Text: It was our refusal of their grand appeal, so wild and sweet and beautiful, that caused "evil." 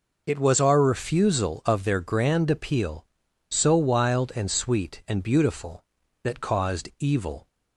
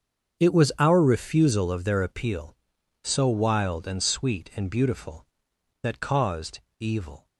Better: first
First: none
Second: starts louder than the rest; strong; until 1.4 s; 7 dB // skips "grand"; at 2.0 s // pauses between "caused" and "evil"; slight; at 6.5 s; 0.20 s long

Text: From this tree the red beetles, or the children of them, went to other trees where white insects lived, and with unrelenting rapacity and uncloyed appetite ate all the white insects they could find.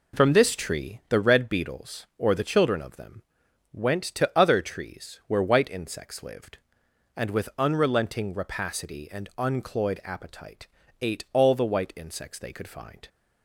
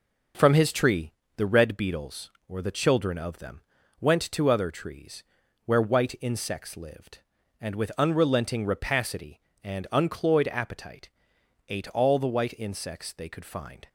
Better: first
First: pauses between "appetite" and "ate"; slight; at 10.6 s; 0.32 s long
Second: says "his" for "this"; at 0.5 s // pauses between "tree" and "the"; slight; at 1.1 s; 0.26 s long // pauses between "trees" and "where"; at 5.2 s; 0.40 s long // pauses between "appetite" and "ate"; noticeable; at 11.0 s; 0.62 s long

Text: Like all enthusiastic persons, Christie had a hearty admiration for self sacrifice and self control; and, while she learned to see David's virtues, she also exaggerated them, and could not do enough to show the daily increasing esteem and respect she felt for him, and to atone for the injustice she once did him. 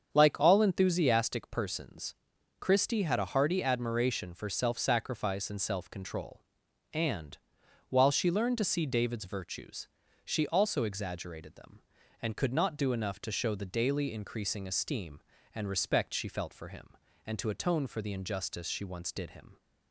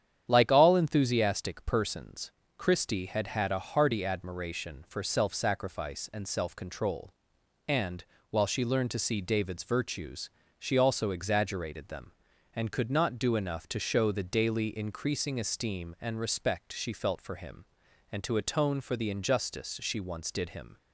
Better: first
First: starts louder than the rest; strong; until 1.1 s; 7 dB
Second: starts louder than the rest; strong; until 1.2 s; 9 dB // says "had" twice; at 3.2 s

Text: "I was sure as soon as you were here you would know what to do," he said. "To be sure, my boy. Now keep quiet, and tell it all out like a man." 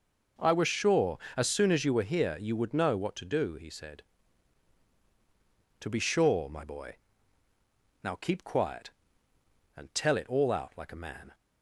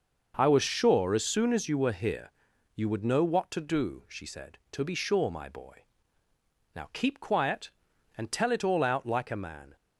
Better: first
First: none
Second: pauses between "here" and "you"; noticeable; at 2.2 s; 0.46 s long // says "she" for "he"; at 4.0 s

